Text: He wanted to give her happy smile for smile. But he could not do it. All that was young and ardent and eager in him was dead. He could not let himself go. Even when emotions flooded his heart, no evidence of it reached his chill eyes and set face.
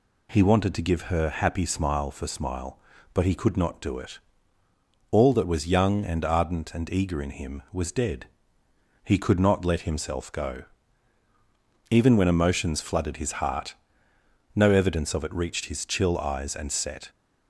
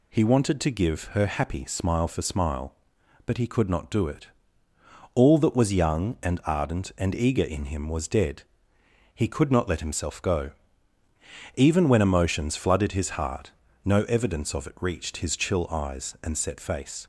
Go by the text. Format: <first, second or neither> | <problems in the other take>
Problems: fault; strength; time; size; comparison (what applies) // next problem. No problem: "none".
second | stops before "face"; at 17.0 s